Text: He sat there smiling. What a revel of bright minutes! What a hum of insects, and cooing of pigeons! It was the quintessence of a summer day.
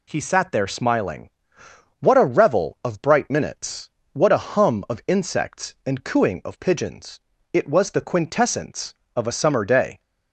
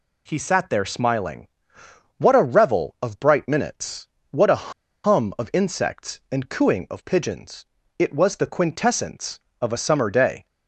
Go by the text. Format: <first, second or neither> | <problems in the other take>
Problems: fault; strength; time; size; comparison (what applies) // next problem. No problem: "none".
first | pauses between "a" and "hum"; slight; at 4.7 s; 0.31 s long